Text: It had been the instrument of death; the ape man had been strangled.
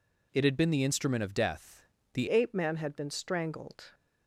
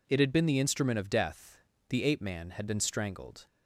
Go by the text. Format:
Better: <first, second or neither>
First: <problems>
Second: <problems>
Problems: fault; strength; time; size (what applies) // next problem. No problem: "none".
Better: second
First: changes voice at "ape"; from 2.2 s on; 1.7 s long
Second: none